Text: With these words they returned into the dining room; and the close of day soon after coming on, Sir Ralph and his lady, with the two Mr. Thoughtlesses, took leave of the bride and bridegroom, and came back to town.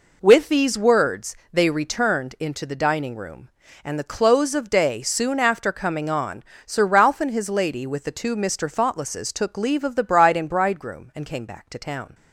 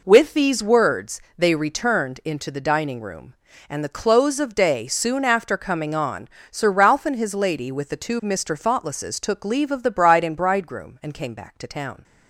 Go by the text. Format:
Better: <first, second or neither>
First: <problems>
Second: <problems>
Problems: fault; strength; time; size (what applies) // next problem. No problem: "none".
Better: neither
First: pauses between "words" and "they"; slight; at 1.3 s; 0.16 s long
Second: pauses between "words" and "they"; slight; at 1.2 s; 0.16 s long